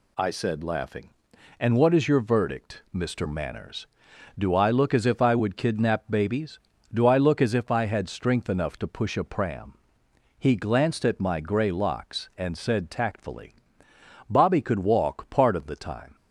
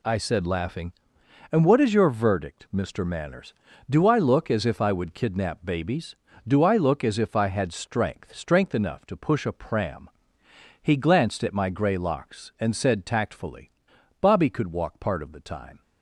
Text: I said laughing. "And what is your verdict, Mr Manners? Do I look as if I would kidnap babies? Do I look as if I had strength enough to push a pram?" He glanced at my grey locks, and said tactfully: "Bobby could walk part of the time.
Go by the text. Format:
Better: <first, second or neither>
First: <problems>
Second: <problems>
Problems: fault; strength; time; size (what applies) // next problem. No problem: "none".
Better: first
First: none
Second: says "strength" twice; at 8.3 s